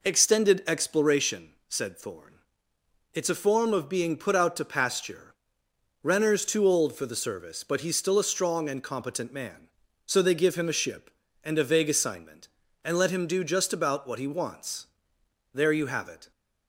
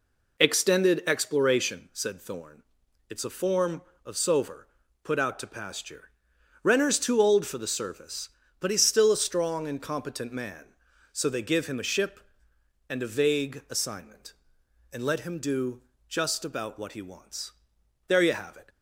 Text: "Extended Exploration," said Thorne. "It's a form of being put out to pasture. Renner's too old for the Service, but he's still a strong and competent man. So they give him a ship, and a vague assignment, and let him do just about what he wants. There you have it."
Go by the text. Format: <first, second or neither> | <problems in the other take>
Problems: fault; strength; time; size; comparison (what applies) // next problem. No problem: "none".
first | says "sover" for "being"; at 4.1 s // pauses between "do" and "just"; slight; at 15.8 s; 0.26 s long